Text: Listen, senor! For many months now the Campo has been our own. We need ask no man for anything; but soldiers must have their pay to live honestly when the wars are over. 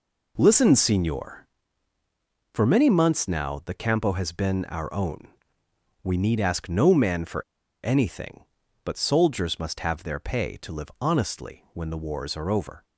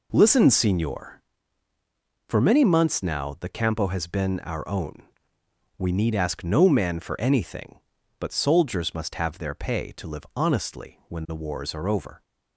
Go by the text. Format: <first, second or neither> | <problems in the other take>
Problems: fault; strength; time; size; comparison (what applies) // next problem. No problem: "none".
second | pauses between "for" and "anything"; at 7.4 s; 0.43 s long